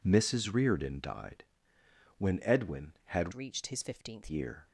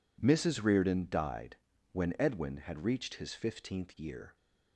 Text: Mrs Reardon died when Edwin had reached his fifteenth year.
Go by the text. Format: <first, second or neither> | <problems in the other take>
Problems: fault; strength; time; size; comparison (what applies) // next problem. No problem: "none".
second | pauses between "died" and "when"; noticeable; at 1.4 s; 0.74 s long; also in the second // changes voice from "reached" to "fifteenth"; from 3.3 to 4.2 s; 0.9 s long